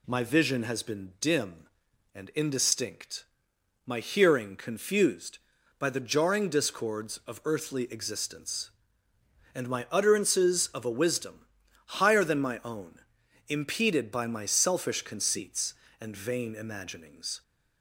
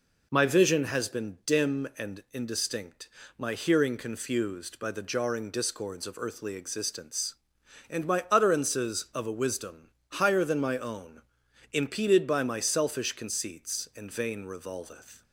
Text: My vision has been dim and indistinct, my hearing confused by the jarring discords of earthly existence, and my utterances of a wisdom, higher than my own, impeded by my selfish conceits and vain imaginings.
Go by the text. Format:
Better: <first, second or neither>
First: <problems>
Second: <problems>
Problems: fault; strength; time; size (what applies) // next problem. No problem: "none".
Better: first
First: none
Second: says "revolveth" for "imaginings"; at 14.4 s